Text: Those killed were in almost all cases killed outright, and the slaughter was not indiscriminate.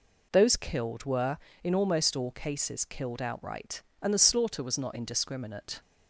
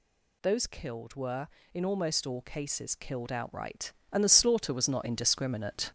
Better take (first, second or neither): first